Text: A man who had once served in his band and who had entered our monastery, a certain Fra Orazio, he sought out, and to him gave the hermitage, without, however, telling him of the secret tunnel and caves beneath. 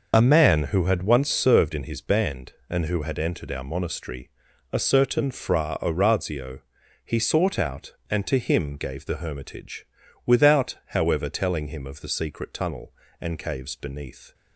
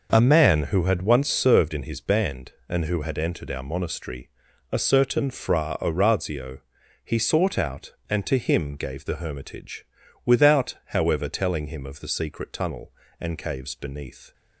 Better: second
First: loses the start of "A"; at 0.1 s; 30 ms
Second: none

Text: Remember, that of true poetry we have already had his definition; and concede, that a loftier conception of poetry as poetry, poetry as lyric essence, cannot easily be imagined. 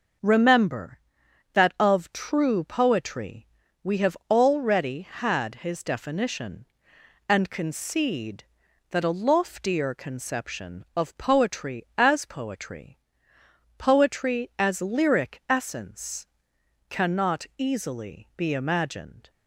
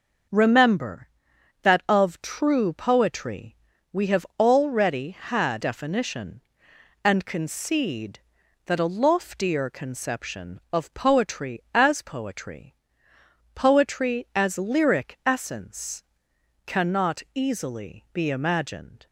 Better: first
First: pauses between "poetry" and "we"; slight; at 3.4 s; 0.36 s long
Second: pauses between "poetry" and "we"; slight; at 3.5 s; 0.36 s long // skips "his"; at 5.6 s

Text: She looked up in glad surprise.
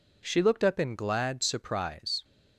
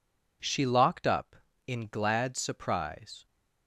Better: first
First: none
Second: says "locked" for "looked"; at 0.6 s

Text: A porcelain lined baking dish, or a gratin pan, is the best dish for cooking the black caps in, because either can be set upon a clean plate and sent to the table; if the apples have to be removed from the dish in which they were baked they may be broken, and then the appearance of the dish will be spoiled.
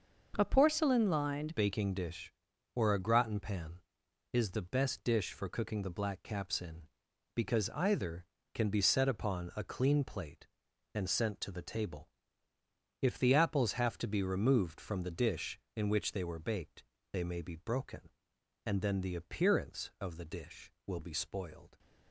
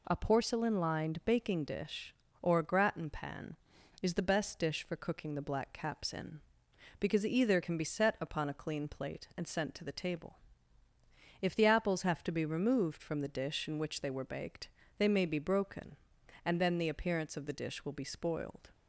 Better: second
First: starts louder than the rest; noticeable; until 1.3 s; 6 dB // changes voice at "baking"; from 1.5 s on; 20.2 s long // pauses between "baked" and "they"; slight; at 16.8 s; 0.28 s long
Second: pauses between "baked" and "they"; slight; at 14.6 s; 0.28 s long

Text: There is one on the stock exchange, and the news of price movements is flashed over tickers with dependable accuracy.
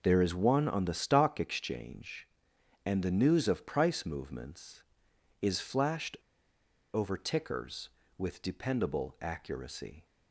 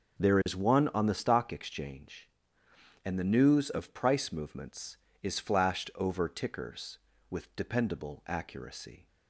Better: second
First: pauses between "flashed" and "over"; noticeable; at 6.1 s; 0.77 s long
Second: none

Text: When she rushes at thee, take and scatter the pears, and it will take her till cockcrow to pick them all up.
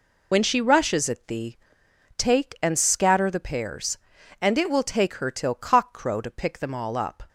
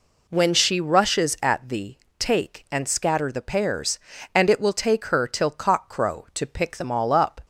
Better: second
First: loses the start of "When"; at 0.3 s; 55 ms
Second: none

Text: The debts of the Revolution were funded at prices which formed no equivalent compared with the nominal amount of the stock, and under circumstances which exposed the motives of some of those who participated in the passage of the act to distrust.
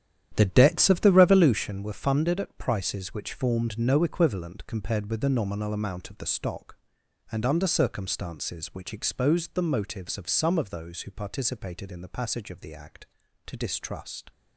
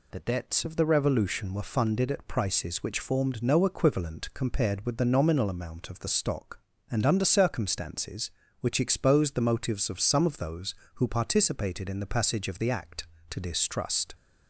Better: second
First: starts louder than the rest; strong; until 1.7 s; 10.5 dB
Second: none

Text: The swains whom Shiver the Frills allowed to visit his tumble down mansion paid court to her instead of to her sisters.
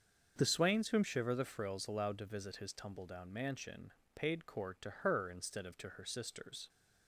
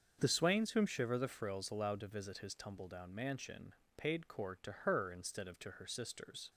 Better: neither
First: starts louder than the rest; until 1.3 s; 6.5 dB // pauses between "mansion" and "paid"; slight; at 3.9 s; 0.24 s long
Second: starts louder than the rest; until 1.2 s; 6.5 dB // pauses between "mansion" and "paid"; slight; at 3.7 s; 0.24 s long

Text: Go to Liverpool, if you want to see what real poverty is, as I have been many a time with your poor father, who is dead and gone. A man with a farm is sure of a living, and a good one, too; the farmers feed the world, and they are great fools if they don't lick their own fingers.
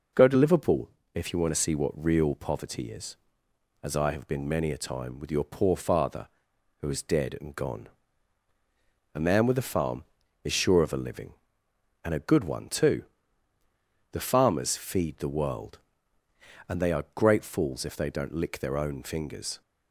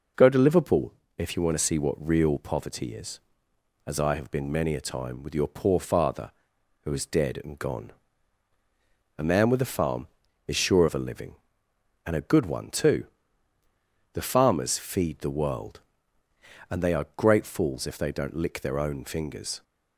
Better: neither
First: none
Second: none

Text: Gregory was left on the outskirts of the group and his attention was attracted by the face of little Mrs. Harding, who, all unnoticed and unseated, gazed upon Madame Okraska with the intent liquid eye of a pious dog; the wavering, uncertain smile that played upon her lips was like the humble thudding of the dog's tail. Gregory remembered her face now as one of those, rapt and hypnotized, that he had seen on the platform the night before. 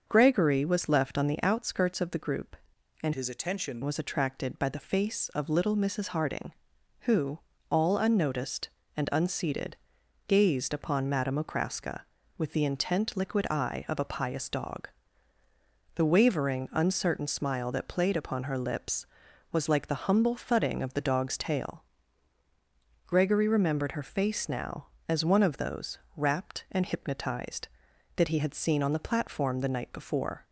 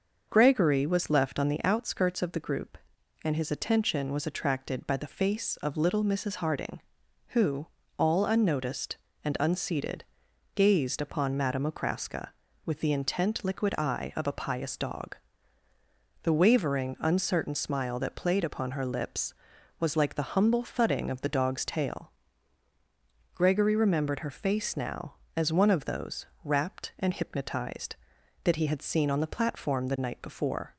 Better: second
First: starts louder than the rest; until 1.0 s; 6.5 dB // changes voice from "his" to "attention"; from 3.1 to 3.8 s; 0.7 s long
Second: starts louder than the rest; noticeable; until 1.3 s; 6 dB

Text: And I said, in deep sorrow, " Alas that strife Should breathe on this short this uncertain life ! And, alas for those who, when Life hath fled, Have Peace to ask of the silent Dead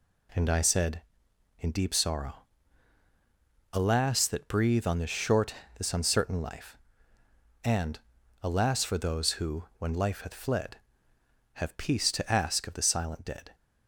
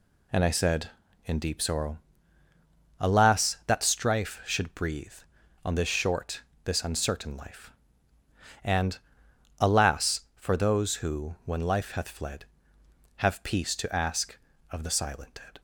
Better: second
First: skips "strife Should"; at 4.4 s // pauses between "short" and "this"; slight; at 5.5 s; 0.22 s long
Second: pauses between "short" and "this"; slight; at 6.4 s; 0.24 s long

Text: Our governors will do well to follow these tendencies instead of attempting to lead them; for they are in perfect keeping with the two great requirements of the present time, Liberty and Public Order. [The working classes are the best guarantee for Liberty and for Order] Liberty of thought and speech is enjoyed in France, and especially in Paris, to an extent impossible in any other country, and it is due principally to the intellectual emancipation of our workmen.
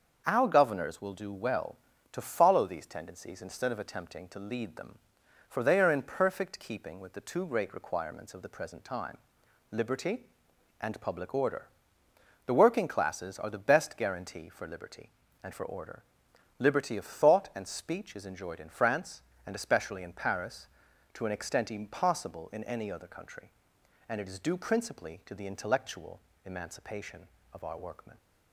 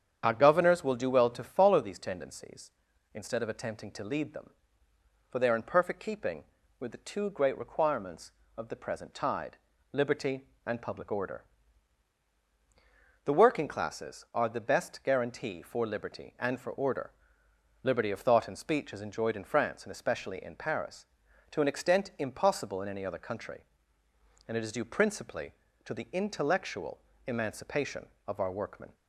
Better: first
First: starts louder than the rest; until 1.2 s; 6.5 dB // pauses between "Order" and "Liberty"; noticeable; at 16.0 s; 0.58 s long // pauses between "intellectual" and "emancipation"; slight; at 26.1 s; 0.26 s long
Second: starts louder than the rest; strong; until 1.2 s; 8.5 dB // says "tide" for "time"; at 9.1 s // pauses between "Order" and "Liberty"; noticeable; at 17.1 s; 0.72 s long // pauses between "intellectual" and "emancipation"; slight; at 27.0 s; 0.26 s long

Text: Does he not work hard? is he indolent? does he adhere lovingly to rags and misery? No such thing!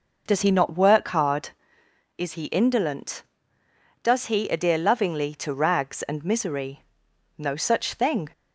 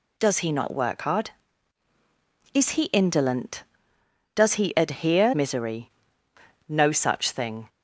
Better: first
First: none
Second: skips "lovingly to rags and"; at 5.3 s

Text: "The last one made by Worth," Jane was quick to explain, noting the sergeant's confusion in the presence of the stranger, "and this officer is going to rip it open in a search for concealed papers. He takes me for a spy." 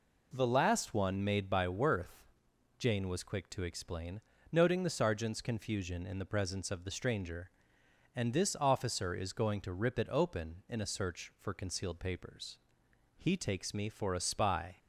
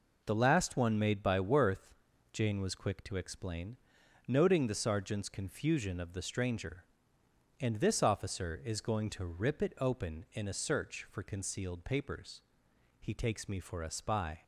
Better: first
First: none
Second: skips "in the presence"; at 5.9 s

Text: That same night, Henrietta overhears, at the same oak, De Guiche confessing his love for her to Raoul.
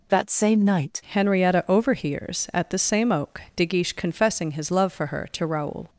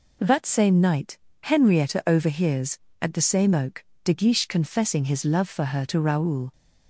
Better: second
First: changes voice at "Henrietta"; from 1.1 s on; 4.7 s long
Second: none

